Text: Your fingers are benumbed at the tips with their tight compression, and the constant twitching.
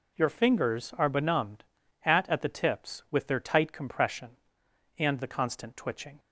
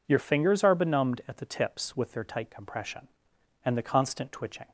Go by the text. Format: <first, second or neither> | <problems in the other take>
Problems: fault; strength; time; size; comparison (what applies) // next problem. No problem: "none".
second | says "at" twice; at 2.2 s